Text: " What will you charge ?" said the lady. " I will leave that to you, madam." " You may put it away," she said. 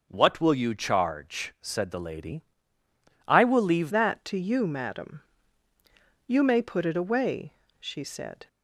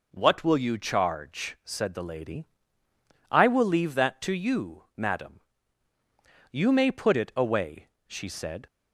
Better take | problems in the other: second | changes voice at "that"; from 3.8 s on; 4.6 s long

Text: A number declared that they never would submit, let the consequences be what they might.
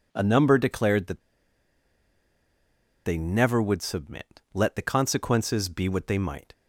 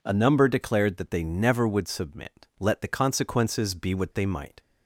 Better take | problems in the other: second | pauses between "that" and "they"; strong; at 1.2 s; 1.8 s long

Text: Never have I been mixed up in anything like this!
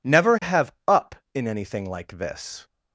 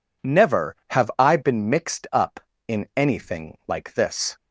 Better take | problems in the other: second | skips "I been mixed"; at 0.8 s

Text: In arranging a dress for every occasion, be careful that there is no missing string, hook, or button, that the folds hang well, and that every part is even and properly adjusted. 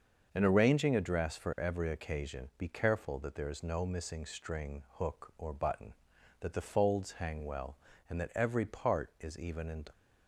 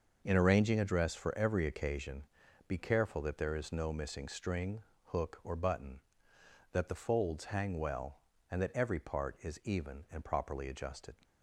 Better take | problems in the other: second | starts louder than the rest; until 1.3 s; 6.5 dB; also in the second // stops before "properly adjusted"; at 9.9 s

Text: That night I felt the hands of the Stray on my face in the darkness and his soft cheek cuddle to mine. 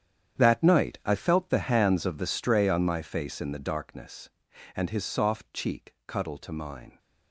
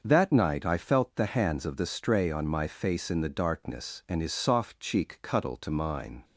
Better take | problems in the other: second | gets quieter; strong; throughout; 15.5 dB // starts louder than the rest; strong; until 1.4 s; 9.5 dB; also in the second

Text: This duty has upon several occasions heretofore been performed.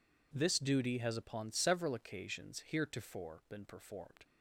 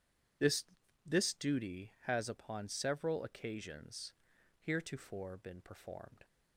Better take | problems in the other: first | says "This" twice; at 1.0 s // pauses between "occasions" and "heretofore"; noticeable; at 4.1 s; 0.50 s long

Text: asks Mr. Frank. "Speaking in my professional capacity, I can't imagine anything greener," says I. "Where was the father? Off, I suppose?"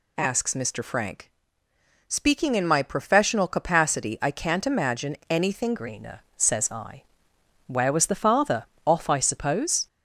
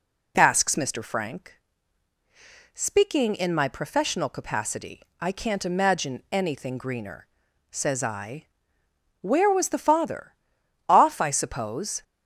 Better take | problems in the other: second | changes voice at "greener"; from 5.7 s on; 4.1 s long

